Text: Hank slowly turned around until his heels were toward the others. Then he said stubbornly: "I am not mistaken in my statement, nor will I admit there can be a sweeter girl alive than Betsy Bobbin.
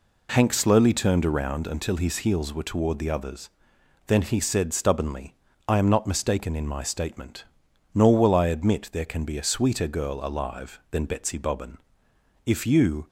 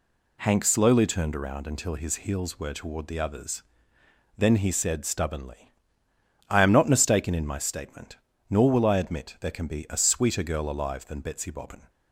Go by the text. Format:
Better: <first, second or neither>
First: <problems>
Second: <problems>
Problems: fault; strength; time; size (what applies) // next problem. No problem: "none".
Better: second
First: goes on to say "If you"; noticeable; from 12.4 s on; 0.62 s long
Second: none